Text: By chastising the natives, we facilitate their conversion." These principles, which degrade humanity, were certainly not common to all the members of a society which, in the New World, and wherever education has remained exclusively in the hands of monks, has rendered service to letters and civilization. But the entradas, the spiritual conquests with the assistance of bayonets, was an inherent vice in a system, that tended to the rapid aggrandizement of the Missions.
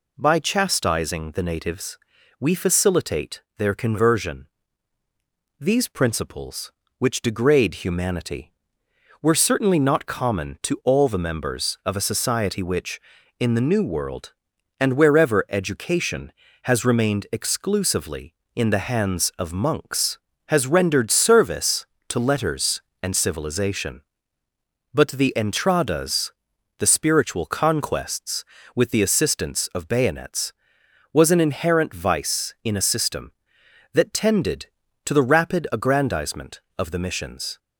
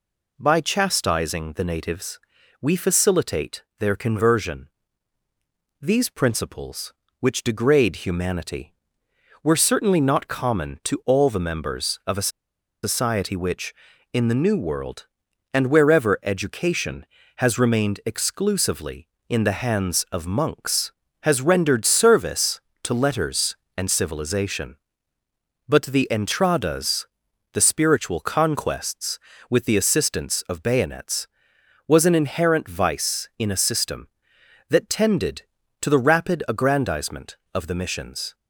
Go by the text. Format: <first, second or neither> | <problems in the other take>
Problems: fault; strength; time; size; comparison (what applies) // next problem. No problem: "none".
first | pauses between "facilitate" and "their"; slight; at 3.6 s; 0.16 s long; slight in the first // pauses between "a" and "society"; noticeable; at 12.2 s; 0.55 s long